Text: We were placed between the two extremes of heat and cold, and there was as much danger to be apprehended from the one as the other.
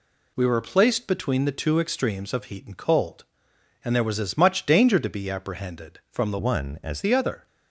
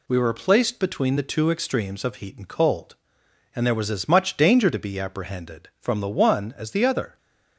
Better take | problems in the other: second | changes voice from "one" to "as"; from 6.3 to 7.0 s; 0.7 s long

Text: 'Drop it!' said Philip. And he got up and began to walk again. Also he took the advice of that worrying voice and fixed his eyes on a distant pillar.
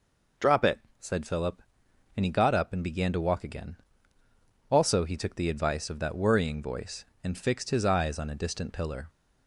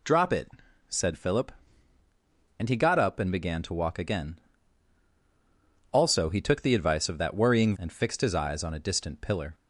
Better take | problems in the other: first | skips "voice"; at 7.7 s

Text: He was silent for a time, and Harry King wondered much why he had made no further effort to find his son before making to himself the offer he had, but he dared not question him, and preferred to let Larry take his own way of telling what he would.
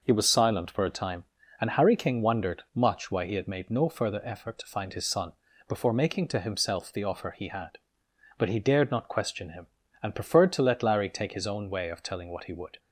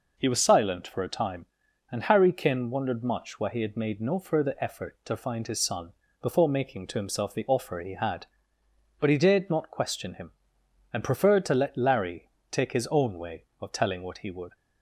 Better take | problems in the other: first | says "Kin" for "King"; at 2.3 s // pauses between "son" and "before"; slight; at 5.9 s; 0.30 s long; slight in the first // pauses between "Larry" and "take"; slight; at 12.2 s; 0.20 s long

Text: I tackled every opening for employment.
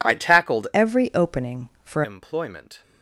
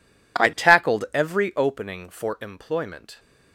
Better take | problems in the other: second | changes voice from "every" to "for"; from 0.7 to 2.0 s; 1.3 s long

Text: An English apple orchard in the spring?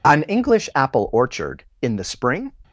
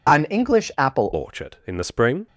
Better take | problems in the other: first | changes voice at "orchard"; from 1.1 s on; 1.1 s long

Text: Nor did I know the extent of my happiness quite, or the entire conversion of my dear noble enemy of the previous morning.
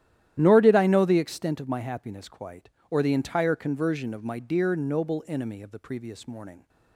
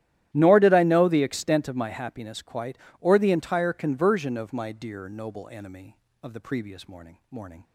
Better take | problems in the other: first | starts louder than the rest; strong; until 1.3 s; 12.5 dB; strong in the first // says "morning" twice; at 7.3 s

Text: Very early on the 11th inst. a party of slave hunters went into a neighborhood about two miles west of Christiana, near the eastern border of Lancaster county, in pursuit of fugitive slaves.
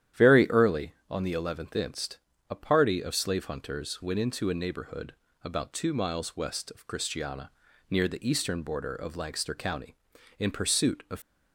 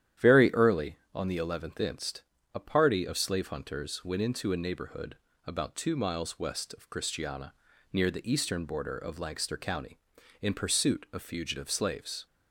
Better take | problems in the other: second | starts louder than the rest; strong; until 1.3 s; 10.5 dB; strong in the second // pauses between "neighborhood" and "about"; slight; at 5.1 s; 0.32 s long; slight in the second // stops before "fugitive slaves"; at 11.2 s

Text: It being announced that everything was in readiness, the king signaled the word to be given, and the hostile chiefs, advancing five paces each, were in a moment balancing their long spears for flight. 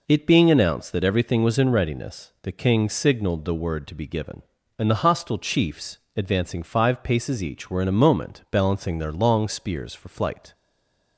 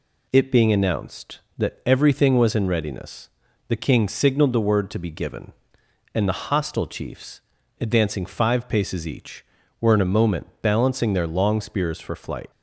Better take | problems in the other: second | stays silent after the last word; slight; from 10.5 s on; 0.6 s long

